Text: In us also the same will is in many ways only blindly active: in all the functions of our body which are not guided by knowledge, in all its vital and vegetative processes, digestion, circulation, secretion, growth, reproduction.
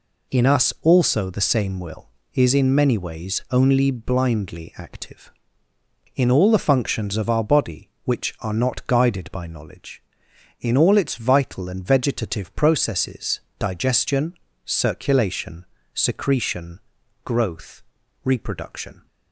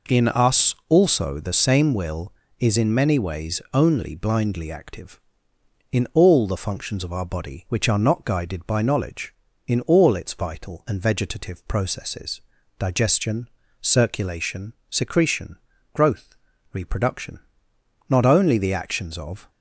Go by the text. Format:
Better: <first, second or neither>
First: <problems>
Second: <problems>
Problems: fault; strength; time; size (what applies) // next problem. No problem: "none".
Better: first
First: none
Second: goes on to say "Not only the actions of"; from 18.0 s on; 1.4 s long